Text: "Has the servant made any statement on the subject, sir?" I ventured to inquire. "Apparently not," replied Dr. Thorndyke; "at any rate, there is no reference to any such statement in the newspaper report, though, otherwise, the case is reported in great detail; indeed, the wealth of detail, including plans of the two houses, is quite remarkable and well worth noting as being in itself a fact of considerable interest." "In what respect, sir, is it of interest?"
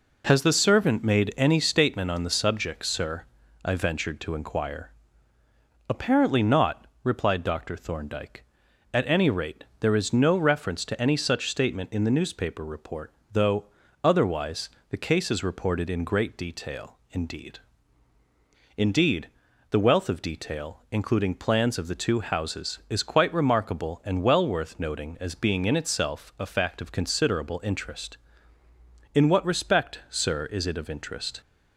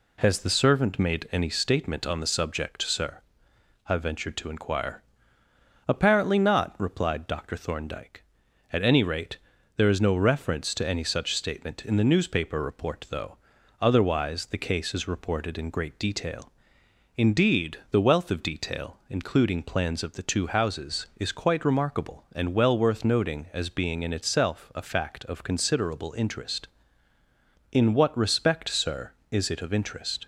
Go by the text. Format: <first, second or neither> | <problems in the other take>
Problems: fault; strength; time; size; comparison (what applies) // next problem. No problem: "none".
second | says "indeed" twice; at 18.7 s